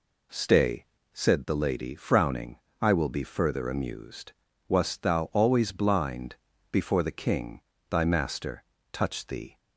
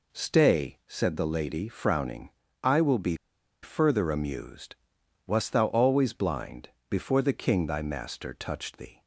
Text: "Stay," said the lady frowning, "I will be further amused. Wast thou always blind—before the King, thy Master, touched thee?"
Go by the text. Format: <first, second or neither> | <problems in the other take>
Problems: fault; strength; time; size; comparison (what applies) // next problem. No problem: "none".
first | pauses between "be" and "further"; noticeable; at 3.1 s; 0.48 s long